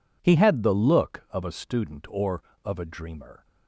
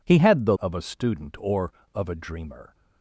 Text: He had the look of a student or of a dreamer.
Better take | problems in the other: first | skips "look"; at 0.5 s

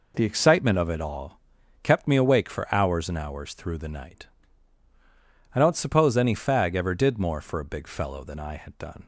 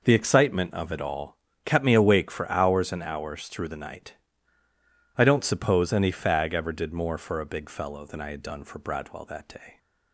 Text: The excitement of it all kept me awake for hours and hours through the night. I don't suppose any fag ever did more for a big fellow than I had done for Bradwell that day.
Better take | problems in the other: second | pauses between "all" and "kept"; at 1.3 s; 0.44 s long; slight in the second // stops before "for Bradwell that day"; at 9.0 s

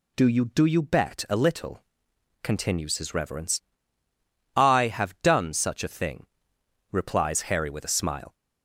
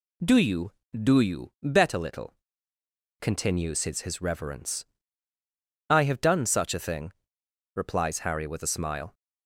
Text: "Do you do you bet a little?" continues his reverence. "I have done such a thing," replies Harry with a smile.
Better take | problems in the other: first | says "his" twice; at 4.0 s

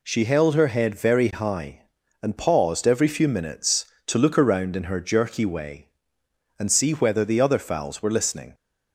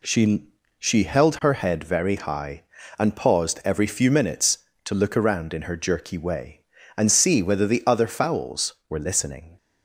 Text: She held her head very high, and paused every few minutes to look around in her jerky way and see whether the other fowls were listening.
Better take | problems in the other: first | says "She" twice; at 0.7 s

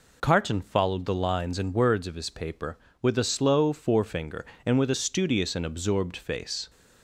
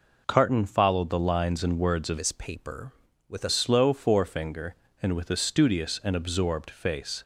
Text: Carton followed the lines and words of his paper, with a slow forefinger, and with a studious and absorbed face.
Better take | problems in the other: first | changes voice from "his" to "a"; from 2.1 to 3.4 s; 1.3 s long

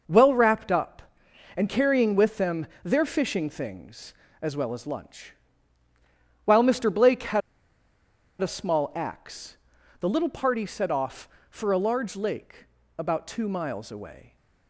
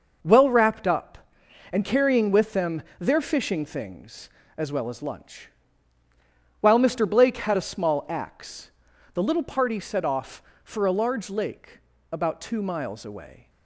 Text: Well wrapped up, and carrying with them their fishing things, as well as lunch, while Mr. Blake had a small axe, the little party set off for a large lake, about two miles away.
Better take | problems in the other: second | pauses between "them" and "their"; slight; at 2.6 s; 0.16 s long; slight in the second // pauses between "had" and "a"; at 7.4 s; 1.0 s long

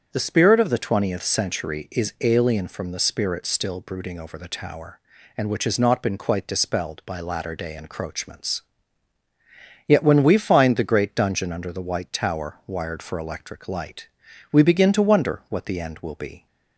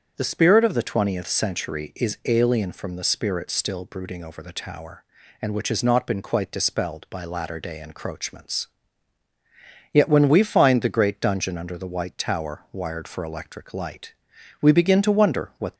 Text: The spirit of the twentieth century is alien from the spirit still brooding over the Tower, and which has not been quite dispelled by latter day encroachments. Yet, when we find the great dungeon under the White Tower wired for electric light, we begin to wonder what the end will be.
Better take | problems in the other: first | starts louder than the rest; strong; until 1.1 s; 7.5 dB; strong in the first // stops before "the end will be"; at 15.7 s

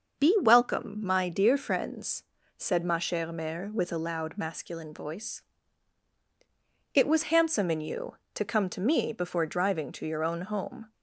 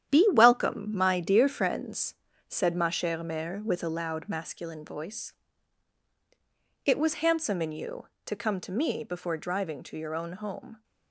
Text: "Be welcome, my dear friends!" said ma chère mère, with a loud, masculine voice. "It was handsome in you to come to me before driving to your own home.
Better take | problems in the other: first | gets quieter; strong; throughout; 8.5 dB // starts louder than the rest; strong; until 1.1 s; 10 dB; also in the first

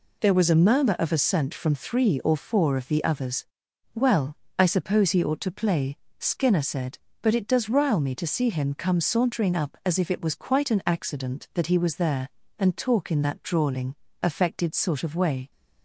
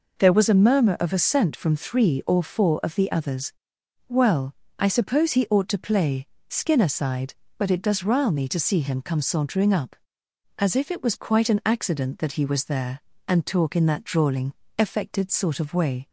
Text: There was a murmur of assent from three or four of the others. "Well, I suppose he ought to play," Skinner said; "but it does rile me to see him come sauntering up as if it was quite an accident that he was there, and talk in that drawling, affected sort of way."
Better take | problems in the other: first | says "sighed" for "said"; at 6.8 s

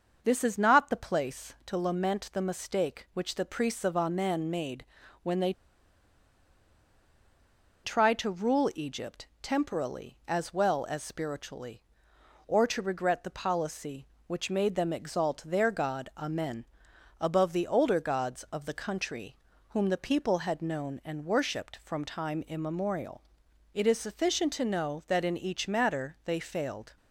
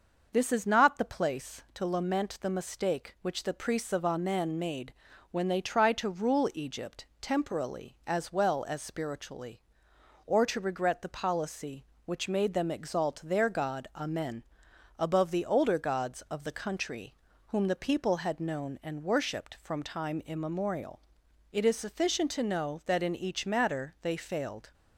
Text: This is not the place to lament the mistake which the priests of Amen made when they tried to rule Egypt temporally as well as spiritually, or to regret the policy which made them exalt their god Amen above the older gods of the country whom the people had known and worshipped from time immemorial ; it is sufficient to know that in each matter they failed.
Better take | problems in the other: second | starts louder than the rest; noticeable; until 1.2 s; 6 dB; noticeable in the second // pauses between "made" and "when"; at 4.8 s; 0.38 s long; also in the second // pauses between "they" and "tried"; strong; at 5.5 s; 2.3 s long // pauses between "Amen" and "above"; noticeable; at 16.6 s; 0.56 s long; noticeable in the second // pauses between "country" and "whom"; slight; at 19.3 s; 0.32 s long; slight in the second

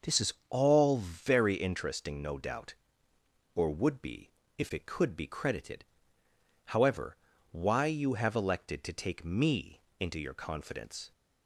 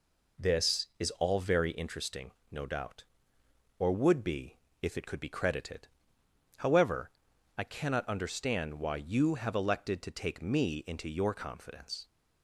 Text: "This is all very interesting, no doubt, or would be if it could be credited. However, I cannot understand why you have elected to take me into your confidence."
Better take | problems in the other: second | starts louder than the rest; until 1.1 s; 6 dB // pauses between "is" and "all"; slight; at 0.3 s; 0.16 s long // pauses between "be" and "if"; slight; at 4.3 s; 0.26 s long; slight in the second // skips "I cannot understand"; at 7.3 s // pauses between "me" and "into"; slight; at 9.8 s; 0.18 s long

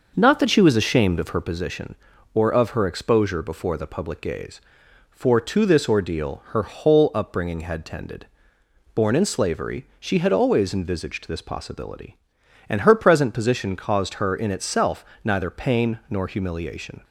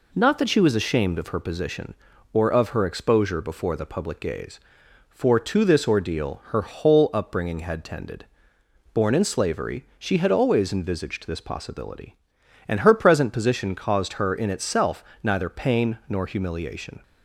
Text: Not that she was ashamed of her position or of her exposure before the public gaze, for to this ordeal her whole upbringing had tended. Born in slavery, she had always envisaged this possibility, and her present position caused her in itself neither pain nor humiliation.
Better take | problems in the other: second | starts louder than the rest; noticeable; until 1.6 s; 6 dB // pauses between "itself" and "neither"; slight; at 15.0 s; 0.20 s long; slight in the second

